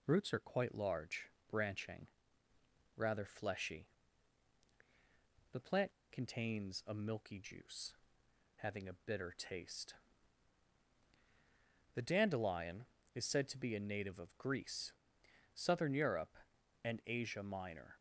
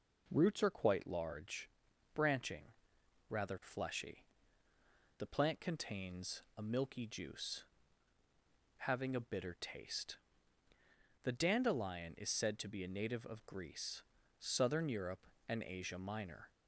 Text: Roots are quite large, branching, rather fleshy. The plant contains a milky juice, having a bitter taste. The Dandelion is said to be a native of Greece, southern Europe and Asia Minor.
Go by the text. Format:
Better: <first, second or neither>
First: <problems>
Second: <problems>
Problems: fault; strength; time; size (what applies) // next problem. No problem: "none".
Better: second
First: pauses between "plant" and "contains"; slight; at 5.9 s; 0.18 s long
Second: none